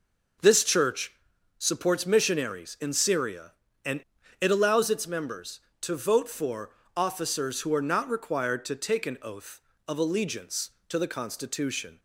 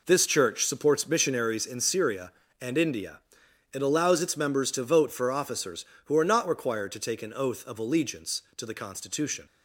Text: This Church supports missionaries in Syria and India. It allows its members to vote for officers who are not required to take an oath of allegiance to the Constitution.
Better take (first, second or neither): second